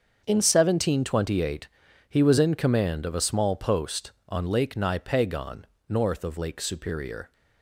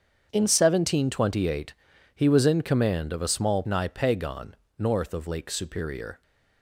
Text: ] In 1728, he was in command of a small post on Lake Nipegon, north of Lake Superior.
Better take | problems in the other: first | starts louder than the rest; strong; until 1.3 s; 7.5 dB; also in the first // skips "post on Lake"; at 3.6 s

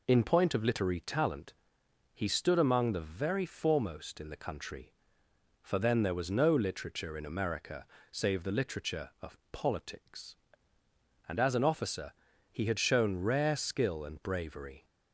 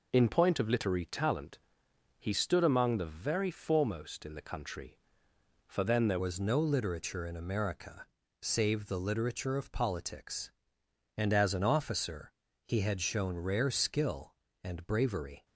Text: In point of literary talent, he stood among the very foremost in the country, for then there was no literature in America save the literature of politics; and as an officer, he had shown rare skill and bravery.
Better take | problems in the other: first | changes voice at "was"; from 6.1 s on; 9.3 s long // pauses between "America" and "save"; slight; at 8.0 s; 0.34 s long; slight in the first

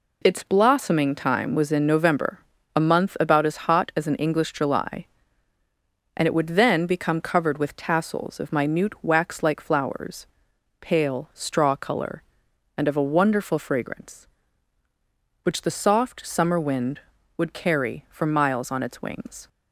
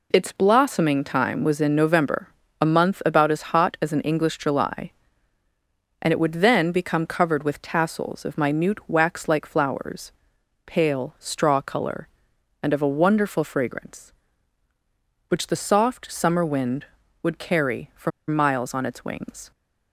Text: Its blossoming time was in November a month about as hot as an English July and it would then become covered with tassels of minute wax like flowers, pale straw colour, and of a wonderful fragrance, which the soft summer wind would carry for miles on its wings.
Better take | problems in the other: first | pauses between "November" and "a"; slight; at 2.2 s; 0.32 s long; slight in the first // pauses between "for" and "miles"; slight; at 18.1 s; 0.18 s long

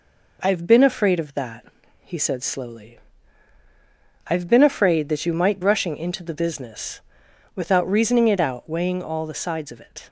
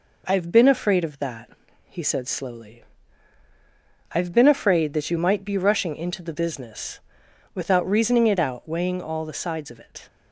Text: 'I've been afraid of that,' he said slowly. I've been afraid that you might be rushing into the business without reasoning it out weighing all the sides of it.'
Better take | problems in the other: second | skips "be"; at 5.6 s // pauses between "business" and "without"; noticeable; at 7.0 s; 0.54 s long; noticeable in the second

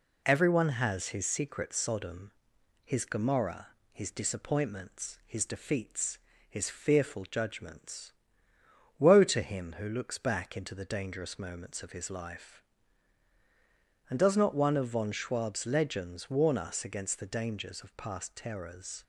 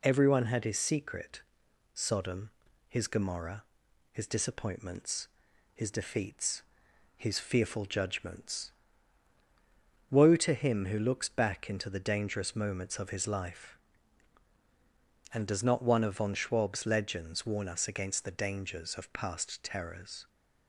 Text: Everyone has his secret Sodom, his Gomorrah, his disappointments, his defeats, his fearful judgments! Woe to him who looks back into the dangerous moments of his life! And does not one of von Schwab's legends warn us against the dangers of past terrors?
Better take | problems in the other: first | says "had" for "has"; at 0.4 s // pauses between "secret" and "Sodom"; noticeable; at 1.4 s; 0.50 s long

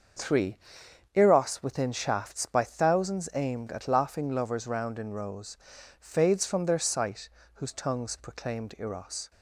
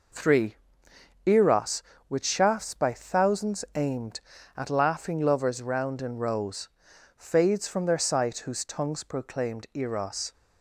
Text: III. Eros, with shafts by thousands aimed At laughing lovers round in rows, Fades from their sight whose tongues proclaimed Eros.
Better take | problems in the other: second | starts louder than the rest; until 1.7 s; 6.5 dB // says "within" for "with"; at 1.6 s // pauses between "sight" and "whose"; slight; at 7.2 s; 0.24 s long

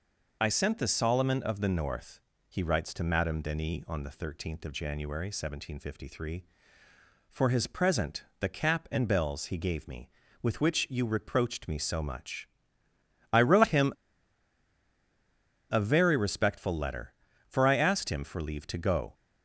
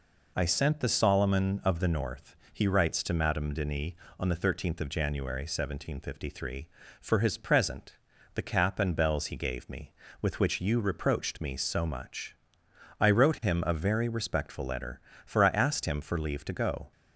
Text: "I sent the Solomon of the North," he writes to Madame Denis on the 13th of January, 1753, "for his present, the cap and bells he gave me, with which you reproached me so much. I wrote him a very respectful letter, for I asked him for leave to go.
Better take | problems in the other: second | pauses between "him" and "a"; strong; at 13.9 s; 1.7 s long

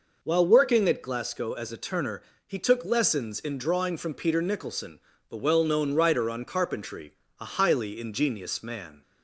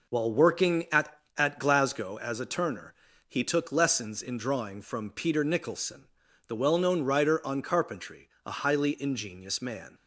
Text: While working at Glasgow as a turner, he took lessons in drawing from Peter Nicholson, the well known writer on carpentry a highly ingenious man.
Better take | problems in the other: first | says "at" twice; at 1.3 s // pauses between "carpentry" and "a"; slight; at 8.2 s; 0.16 s long; slight in the first

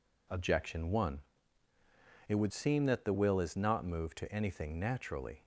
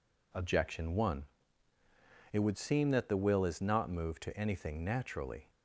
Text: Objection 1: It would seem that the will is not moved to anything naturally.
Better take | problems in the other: neither | none

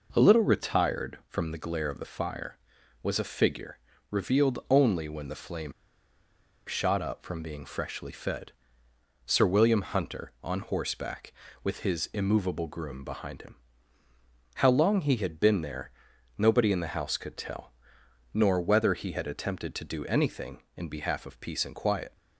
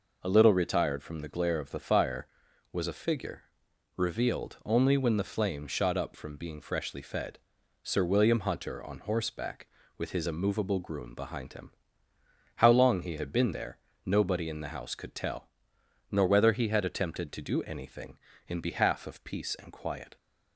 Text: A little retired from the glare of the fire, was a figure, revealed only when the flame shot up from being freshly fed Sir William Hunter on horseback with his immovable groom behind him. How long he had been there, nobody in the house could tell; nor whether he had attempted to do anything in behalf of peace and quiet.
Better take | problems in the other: second | pauses between "flame" and "shot"; noticeable; at 5.7 s; 0.95 s long // pauses between "fed" and "Sir"; noticeable; at 8.5 s; 0.74 s long; also in the second

